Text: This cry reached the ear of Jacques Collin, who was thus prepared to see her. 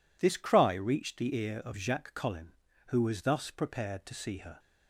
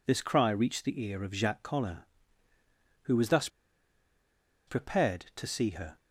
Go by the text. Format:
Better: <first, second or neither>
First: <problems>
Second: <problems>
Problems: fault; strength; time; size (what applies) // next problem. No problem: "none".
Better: first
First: none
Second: pauses between "thus" and "prepared"; at 3.4 s; 1.1 s long